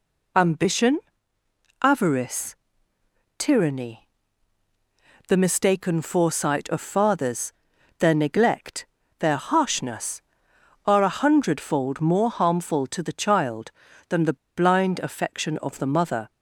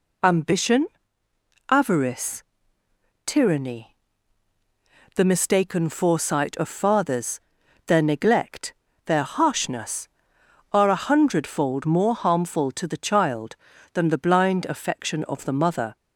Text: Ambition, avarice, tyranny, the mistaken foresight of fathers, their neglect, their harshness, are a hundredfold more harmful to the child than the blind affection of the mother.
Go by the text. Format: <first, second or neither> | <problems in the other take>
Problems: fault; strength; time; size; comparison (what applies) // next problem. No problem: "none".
second | pauses between "the" and "blind"; slight; at 14.3 s; 0.19 s long